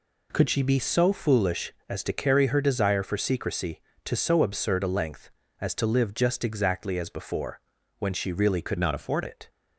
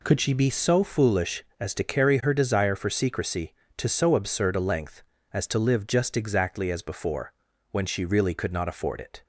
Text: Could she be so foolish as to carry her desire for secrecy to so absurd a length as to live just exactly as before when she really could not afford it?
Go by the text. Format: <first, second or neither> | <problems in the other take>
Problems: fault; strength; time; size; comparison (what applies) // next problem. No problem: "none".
second | pauses between "before" and "when"; at 7.5 s; 0.40 s long; also in the second // changes voice from "not" to "afford"; from 8.7 to 9.2 s; 0.5 s long